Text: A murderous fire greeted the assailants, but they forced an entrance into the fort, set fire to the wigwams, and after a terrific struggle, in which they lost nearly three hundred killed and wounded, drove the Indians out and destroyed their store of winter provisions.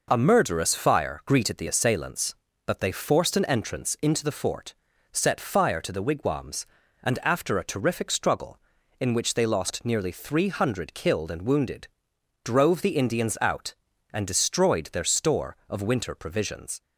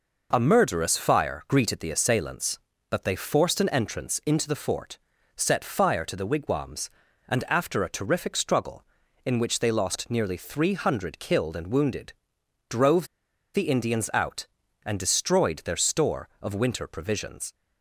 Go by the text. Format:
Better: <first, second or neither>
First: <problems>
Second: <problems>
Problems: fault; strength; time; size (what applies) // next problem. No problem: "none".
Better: first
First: none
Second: pauses between "drove" and "the"; noticeable; at 13.0 s; 0.47 s long